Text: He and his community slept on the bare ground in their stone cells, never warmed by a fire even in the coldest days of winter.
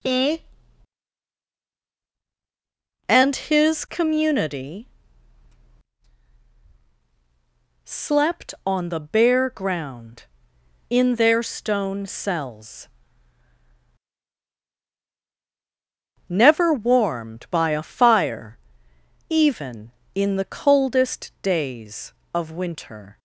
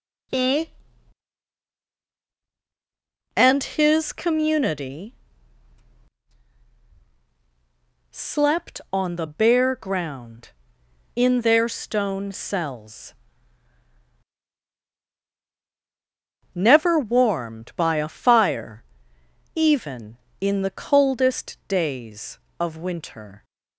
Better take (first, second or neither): neither